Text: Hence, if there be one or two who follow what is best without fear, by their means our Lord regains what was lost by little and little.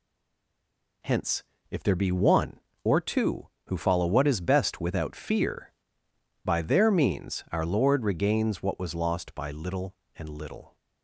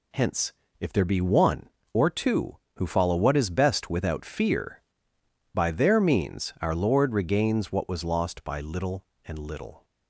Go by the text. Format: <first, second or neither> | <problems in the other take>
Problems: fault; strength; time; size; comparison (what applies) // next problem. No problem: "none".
second | stays silent before the first word; until 1.0 s; 1.0 s long